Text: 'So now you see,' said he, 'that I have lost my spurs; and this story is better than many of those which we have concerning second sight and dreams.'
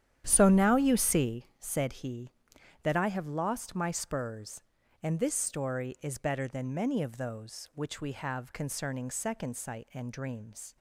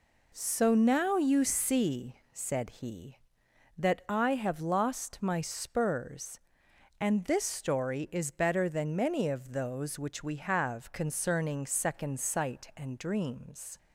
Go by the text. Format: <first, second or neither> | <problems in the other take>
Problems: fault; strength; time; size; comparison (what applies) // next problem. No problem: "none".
second | starts louder than the rest; strong; until 1.7 s; 10 dB